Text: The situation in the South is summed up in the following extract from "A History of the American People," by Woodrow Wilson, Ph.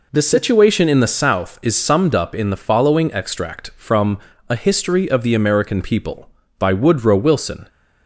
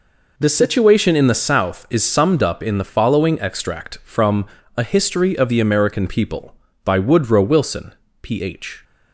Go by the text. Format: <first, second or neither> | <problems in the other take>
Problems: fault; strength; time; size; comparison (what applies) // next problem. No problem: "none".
second | pauses between "from" and "A"; slight; at 4.1 s; 0.30 s long; slight in the second // stops before "Ph"; at 7.6 s